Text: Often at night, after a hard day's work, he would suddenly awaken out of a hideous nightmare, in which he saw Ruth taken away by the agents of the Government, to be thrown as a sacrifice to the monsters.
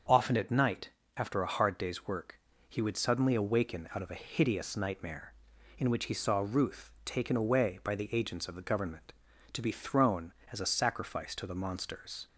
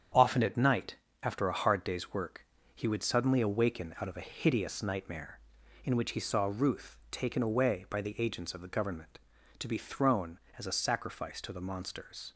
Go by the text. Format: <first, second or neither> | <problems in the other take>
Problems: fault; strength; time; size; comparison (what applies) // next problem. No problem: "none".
first | gets quieter; noticeable; throughout; 6 dB // starts louder than the rest; strong; until 1.4 s; 8 dB; also in the first